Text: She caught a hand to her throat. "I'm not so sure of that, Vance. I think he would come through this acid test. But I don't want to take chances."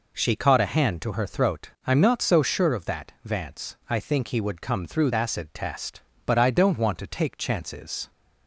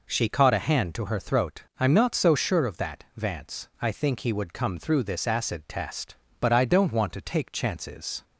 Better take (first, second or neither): second